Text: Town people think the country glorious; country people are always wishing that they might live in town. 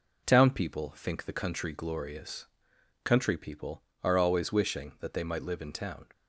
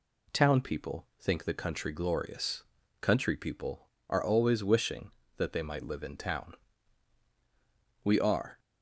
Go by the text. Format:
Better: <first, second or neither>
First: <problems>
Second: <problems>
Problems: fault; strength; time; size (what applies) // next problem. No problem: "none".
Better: first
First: none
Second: goes on to say "We are"; from 8.0 s on; 0.56 s long